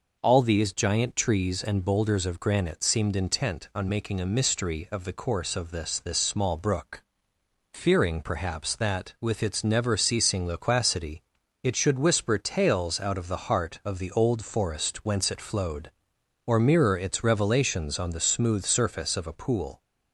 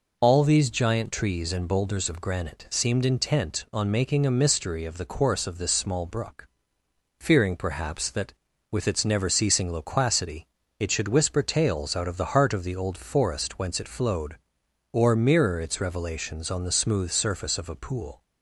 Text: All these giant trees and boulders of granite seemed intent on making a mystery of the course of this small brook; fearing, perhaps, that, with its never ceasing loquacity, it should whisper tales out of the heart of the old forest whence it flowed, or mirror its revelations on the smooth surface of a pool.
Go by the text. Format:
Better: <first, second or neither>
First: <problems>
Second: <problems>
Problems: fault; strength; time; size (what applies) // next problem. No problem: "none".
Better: second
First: says "this" twice; at 5.9 s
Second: none